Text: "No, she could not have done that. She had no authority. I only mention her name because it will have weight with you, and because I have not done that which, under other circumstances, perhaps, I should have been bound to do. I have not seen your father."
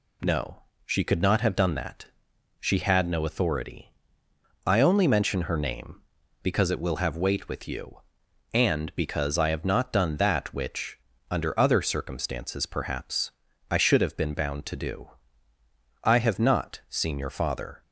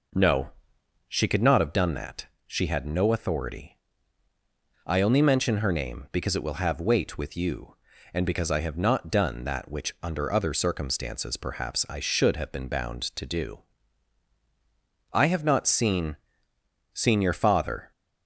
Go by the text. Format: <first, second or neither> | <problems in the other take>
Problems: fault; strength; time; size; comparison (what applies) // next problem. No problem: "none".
first | says "seen" twice; at 16.9 s